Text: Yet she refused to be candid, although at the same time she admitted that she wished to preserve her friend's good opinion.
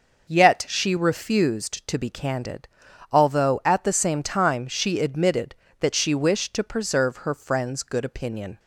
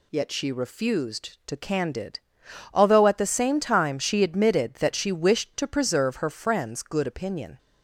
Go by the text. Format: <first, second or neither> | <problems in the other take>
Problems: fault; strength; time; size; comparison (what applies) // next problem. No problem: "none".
first | skips "be"; at 1.5 s